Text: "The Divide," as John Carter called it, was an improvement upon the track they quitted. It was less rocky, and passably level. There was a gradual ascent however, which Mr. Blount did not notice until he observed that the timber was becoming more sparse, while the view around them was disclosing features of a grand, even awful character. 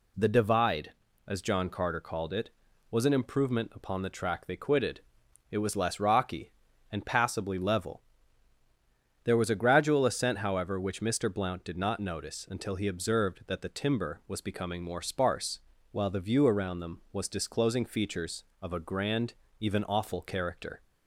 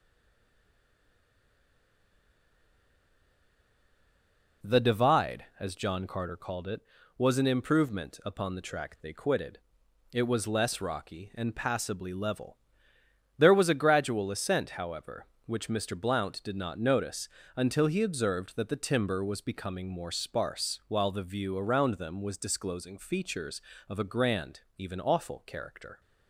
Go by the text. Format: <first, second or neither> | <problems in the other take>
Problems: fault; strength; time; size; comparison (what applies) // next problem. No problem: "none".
first | stays silent before the first word; strong; until 4.6 s; 4.6 s long // pauses between "notice" and "until"; slight; at 17.2 s; 0.28 s long